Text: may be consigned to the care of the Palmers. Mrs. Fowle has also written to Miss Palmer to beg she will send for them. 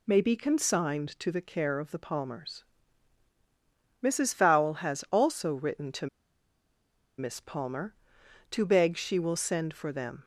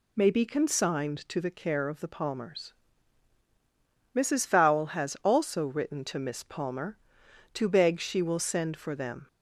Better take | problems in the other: second | pauses between "to" and "Miss"; at 6.0 s; 1.1 s long

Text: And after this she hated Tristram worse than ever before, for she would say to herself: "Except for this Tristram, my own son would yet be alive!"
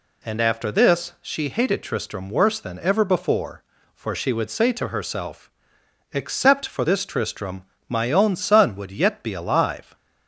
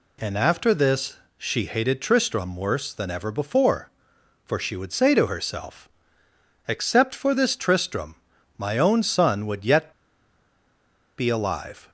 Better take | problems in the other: first | pauses between "this" and "she"; slight; at 1.1 s; 0.20 s long // pauses between "yet" and "be"; strong; at 9.9 s; 1.2 s long

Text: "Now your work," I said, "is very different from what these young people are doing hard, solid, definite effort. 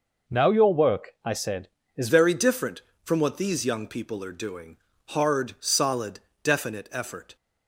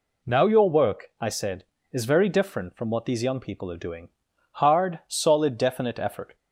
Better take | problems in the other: second | changes voice at "very"; from 2.0 s on; 5.3 s long // pauses between "doing" and "hard"; slight; at 4.7 s; 0.32 s long; also in the second

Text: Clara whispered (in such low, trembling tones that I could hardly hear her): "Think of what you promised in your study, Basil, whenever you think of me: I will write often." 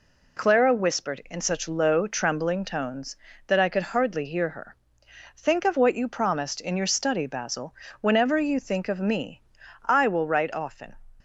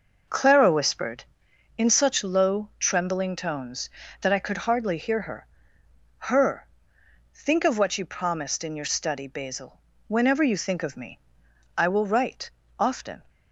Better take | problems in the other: first | says "her" twice; at 6.1 s // pauses between "write" and "often"; slight; at 12.5 s; 0.26 s long

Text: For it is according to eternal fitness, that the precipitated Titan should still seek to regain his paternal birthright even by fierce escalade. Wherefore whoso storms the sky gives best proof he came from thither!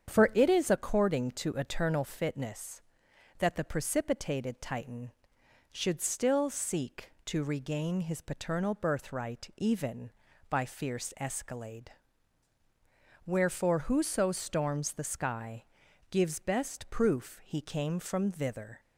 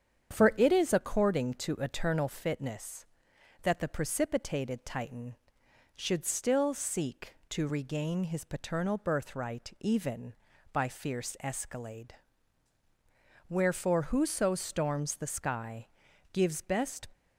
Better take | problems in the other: first | starts louder than the rest; strong; until 1.3 s; 8 dB; strong in the first // pauses between "sky" and "gives"; at 15.8 s; 0.43 s long; also in the first // stops before "proof he came from thither"; at 17.1 s

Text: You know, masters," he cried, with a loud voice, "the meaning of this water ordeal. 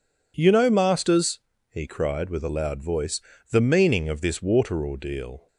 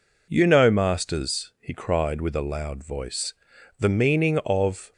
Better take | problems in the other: first | stops before "this water ordeal"; at 4.9 s

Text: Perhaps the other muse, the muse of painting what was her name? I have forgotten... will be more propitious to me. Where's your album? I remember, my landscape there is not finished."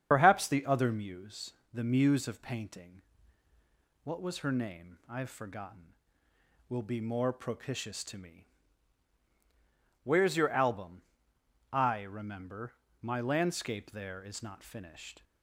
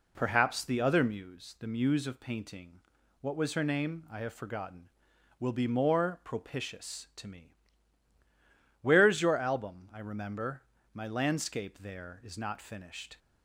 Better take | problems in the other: second | loses the start of "Perhaps"; at 0.1 s; 65 ms // starts louder than the rest; strong; until 1.1 s; 8 dB // pauses between "painting" and "what"; at 3.0 s; 1.0 s long; also in the second

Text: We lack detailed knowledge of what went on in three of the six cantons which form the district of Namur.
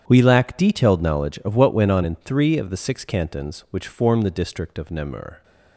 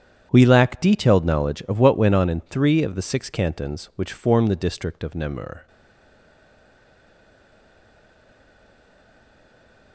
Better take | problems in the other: first | starts louder than the rest; strong; until 1.3 s; 9 dB; strong in the first // stays silent after the last word; strong; from 5.6 s on; 4.3 s long

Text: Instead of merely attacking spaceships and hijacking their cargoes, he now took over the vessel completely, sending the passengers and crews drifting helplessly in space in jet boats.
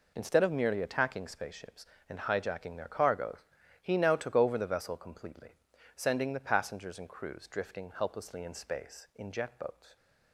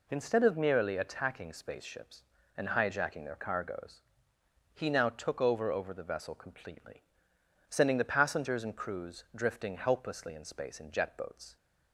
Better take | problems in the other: first | says "over" twice; at 5.7 s

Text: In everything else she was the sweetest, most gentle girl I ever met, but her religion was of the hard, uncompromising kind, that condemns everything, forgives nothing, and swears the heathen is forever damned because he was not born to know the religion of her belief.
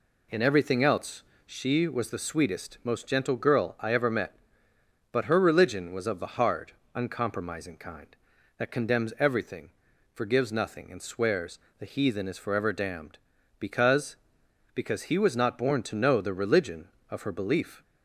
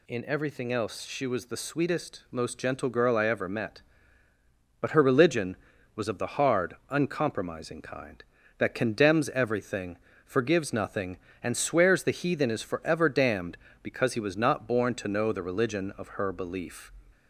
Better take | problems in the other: second | pauses between "else" and "she"; slight; at 1.2 s; 0.24 s long // pauses between "swears" and "the"; slight; at 11.5 s; 0.22 s long // says "because" twice; at 14.7 s

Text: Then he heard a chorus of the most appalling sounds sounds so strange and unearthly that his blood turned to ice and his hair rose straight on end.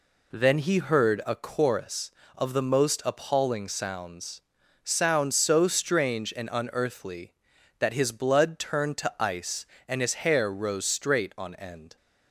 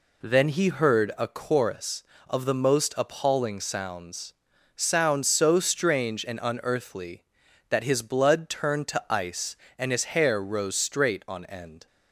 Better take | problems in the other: neither | pauses between "sounds" and "sounds"; the same in both

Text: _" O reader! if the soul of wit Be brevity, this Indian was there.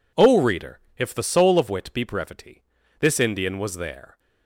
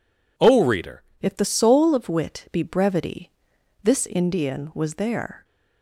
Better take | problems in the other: first | changes voice at "if"; from 1.1 s on; 4.3 s long

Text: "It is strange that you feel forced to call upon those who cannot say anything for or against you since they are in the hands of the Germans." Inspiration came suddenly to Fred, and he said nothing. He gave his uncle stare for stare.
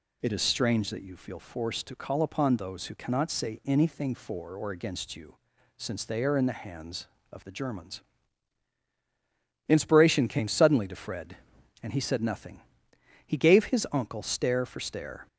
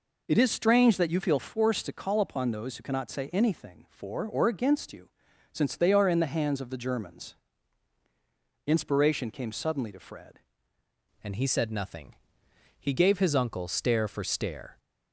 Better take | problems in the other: first | pauses between "you" and "since"; at 5.0 s; 0.42 s long; also in the first // changes voice at "and"; from 11.2 s on; 3.5 s long

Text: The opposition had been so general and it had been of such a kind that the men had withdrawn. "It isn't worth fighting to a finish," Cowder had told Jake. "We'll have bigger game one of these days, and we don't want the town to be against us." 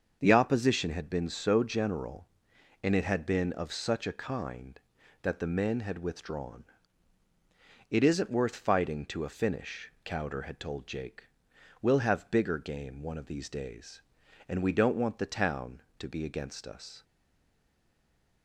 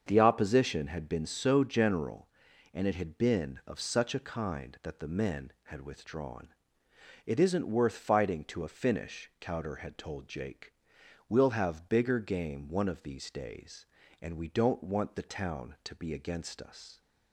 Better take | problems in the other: second | starts louder than the rest; until 1.2 s; 6.5 dB; also in the second // stays silent after the last word; noticeable; from 17.0 s on; 1.4 s long

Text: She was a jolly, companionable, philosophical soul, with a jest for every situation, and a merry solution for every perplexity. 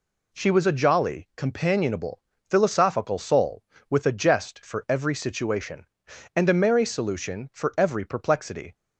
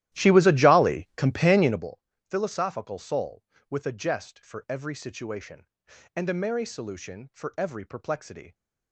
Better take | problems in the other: first | starts louder than the rest; strong; until 1.9 s; 14 dB

